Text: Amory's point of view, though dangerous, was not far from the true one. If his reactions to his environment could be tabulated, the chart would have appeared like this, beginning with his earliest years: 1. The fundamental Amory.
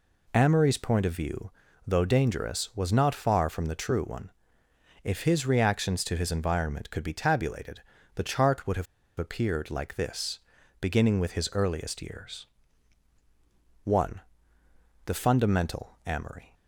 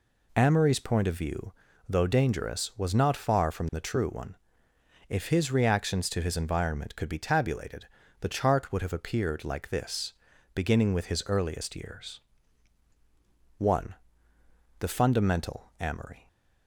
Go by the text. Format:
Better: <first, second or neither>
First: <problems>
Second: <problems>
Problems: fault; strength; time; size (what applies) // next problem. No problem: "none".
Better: second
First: pauses between "have" and "appeared"; slight; at 8.8 s; 0.33 s long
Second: none